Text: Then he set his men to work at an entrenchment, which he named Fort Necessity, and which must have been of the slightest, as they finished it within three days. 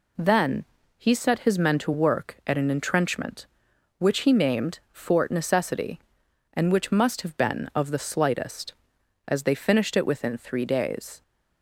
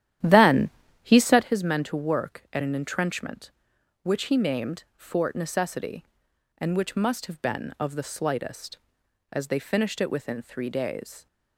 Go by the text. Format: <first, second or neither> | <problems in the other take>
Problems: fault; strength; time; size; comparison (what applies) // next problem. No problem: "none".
first | starts louder than the rest; strong; until 1.5 s; 11.5 dB // pauses between "Then" and "he"; slight; at 0.7 s; 0.32 s long; slight in the first